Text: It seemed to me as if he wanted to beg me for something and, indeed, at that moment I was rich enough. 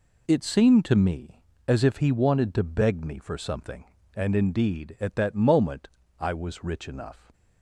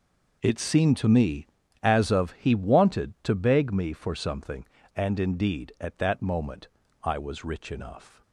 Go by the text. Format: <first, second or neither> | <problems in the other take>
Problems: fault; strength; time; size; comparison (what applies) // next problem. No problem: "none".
first | says "of" for "if"; at 2.1 s // pauses between "moment" and "I"; slight; at 6.6 s; 0.34 s long; slight in the first